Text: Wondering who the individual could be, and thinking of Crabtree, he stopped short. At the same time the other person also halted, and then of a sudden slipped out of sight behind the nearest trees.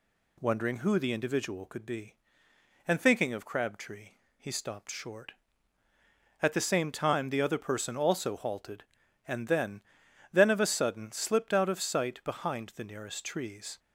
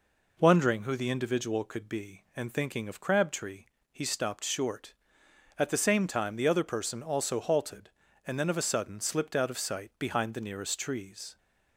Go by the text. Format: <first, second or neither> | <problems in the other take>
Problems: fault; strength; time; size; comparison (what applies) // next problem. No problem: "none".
second | says "then" twice; at 10.3 s